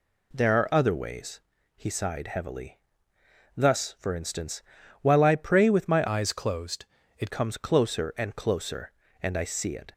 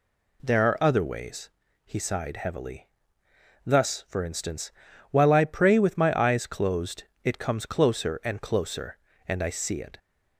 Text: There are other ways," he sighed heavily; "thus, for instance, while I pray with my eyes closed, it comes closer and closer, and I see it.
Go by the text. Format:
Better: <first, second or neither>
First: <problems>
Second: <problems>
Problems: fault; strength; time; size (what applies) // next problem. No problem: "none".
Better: second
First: changes voice from "eyes" to "it"; from 6.0 to 7.3 s; 1.3 s long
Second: none